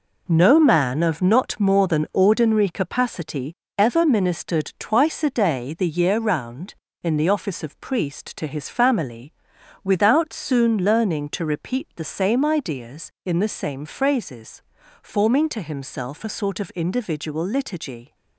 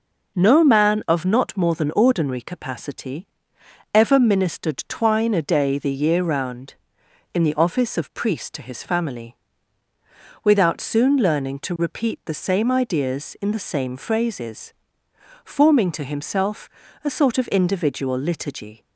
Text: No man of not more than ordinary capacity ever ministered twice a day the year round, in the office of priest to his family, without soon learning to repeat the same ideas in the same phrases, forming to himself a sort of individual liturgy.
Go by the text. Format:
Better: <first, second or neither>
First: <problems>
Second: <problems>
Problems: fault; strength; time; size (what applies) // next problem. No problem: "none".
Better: first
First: pauses between "capacity" and "ever"; slight; at 3.5 s; 0.24 s long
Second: pauses between "capacity" and "ever"; noticeable; at 3.2 s; 0.66 s long // says "twine" for "twice"; at 4.8 s // pauses between "himself" and "a"; slight; at 16.6 s; 0.36 s long